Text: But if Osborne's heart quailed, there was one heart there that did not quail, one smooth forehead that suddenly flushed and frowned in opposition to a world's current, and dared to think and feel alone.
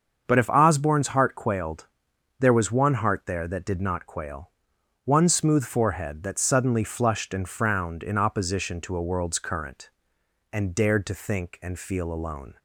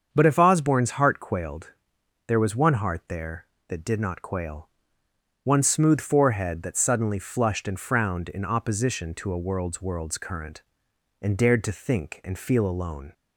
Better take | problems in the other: first | starts louder than the rest; until 1.1 s; 7 dB; also in the first // says "world's" twice; at 9.8 s

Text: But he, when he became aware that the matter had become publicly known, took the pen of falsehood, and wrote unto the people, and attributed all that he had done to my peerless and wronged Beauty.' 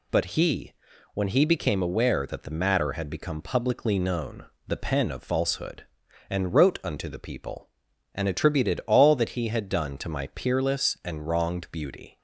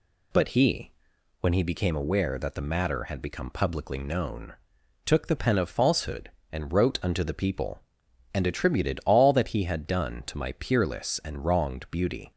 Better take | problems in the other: second | skips "took"; at 4.5 s

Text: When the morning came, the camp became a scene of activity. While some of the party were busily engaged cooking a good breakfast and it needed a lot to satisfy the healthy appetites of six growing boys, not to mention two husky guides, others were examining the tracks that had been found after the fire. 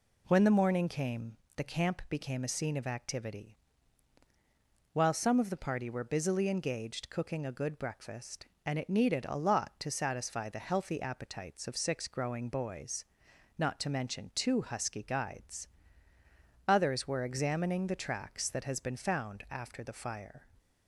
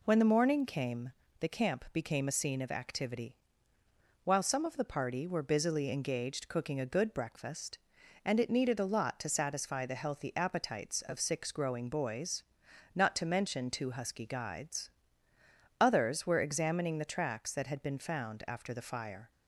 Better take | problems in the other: second | says "has" for "had"; at 18.6 s

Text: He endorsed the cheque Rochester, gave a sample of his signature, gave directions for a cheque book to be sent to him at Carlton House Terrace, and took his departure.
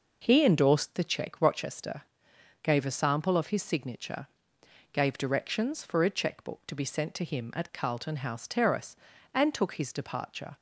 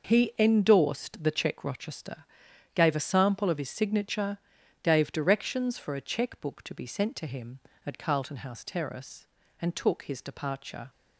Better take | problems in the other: neither | none

